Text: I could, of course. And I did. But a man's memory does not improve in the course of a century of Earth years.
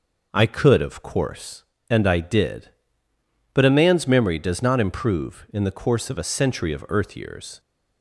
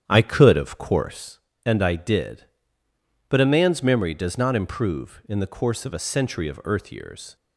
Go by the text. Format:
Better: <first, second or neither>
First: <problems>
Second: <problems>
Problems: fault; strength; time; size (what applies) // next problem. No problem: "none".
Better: first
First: none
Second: starts louder than the rest; strong; until 1.3 s; 9.5 dB